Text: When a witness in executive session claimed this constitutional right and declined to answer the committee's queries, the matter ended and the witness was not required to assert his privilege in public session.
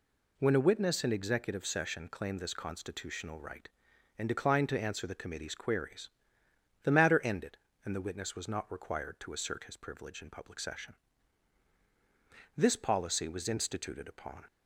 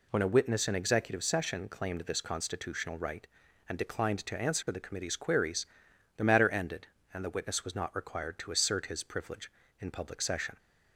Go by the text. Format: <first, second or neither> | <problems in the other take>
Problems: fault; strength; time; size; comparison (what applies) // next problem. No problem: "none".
second | goes on to say "This policy was instituted upon"; strong; from 12.5 s on; 1.8 s long